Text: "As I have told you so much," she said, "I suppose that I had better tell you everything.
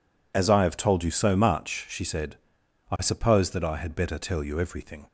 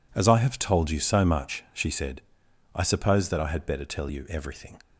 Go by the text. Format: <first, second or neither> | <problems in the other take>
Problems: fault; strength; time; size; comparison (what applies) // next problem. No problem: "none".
neither | none